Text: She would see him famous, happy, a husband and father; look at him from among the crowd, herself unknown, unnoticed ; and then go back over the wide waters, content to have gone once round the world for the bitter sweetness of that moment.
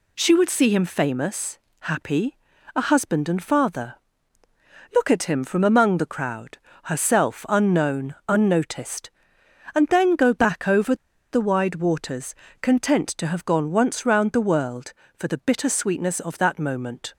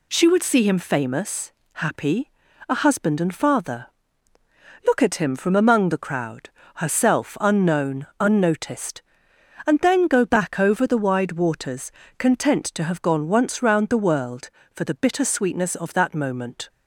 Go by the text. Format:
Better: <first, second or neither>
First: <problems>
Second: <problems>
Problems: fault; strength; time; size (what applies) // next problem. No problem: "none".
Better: second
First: pauses between "over" and "the"; at 10.9 s; 0.37 s long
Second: none